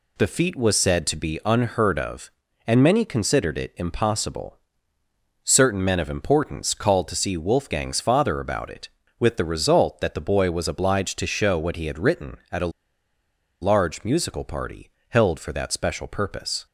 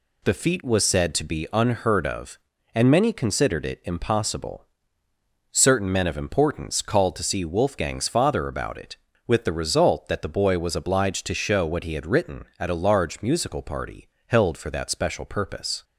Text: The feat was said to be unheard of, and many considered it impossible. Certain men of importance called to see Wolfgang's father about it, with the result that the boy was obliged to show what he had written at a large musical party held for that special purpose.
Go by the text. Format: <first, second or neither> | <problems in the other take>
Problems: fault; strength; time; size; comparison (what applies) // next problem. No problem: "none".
second | pauses between "a" and "large"; noticeable; at 12.7 s; 0.91 s long // pauses between "party" and "held"; slight; at 14.8 s; 0.20 s long; slight in the second